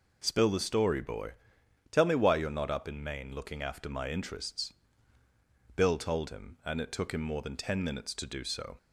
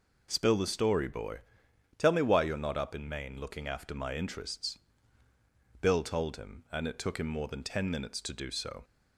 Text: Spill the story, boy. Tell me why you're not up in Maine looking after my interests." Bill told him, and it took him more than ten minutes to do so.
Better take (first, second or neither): neither